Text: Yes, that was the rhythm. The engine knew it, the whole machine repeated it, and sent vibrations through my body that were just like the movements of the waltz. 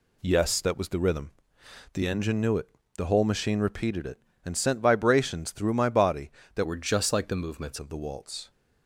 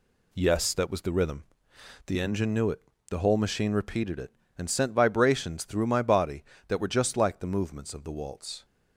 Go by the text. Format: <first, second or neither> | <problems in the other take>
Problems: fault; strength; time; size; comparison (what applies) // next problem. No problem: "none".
second | changes voice from "were" to "movements"; from 6.6 to 7.7 s; 1.1 s long